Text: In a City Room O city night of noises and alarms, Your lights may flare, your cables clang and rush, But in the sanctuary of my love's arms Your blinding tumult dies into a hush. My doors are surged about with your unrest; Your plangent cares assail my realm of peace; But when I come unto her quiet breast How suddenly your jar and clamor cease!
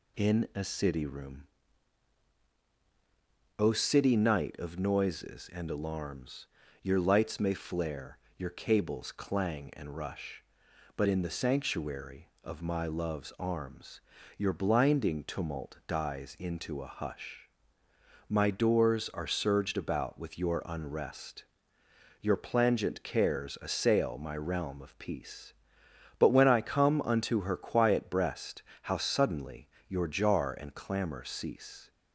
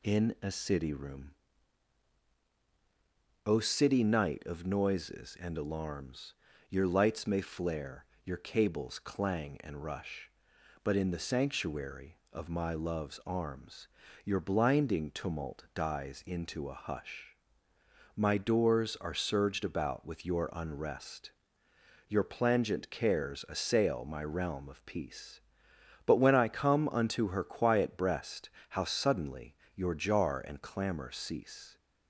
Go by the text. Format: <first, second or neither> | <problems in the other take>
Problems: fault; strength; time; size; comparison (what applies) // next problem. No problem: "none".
neither | pauses between "Room" and "O"; strong; the same in both // pauses between "arms" and "Your"; slight; the same in both // pauses between "breast" and "How"; slight; the same in both // pauses between "suddenly" and "your"; slight; the same in both